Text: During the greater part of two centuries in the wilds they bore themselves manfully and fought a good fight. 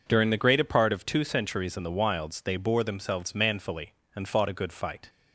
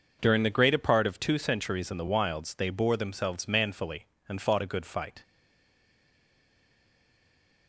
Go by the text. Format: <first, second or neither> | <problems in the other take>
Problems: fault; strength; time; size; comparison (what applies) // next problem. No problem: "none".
first | stays silent after the last word; from 5.2 s on; 2.4 s long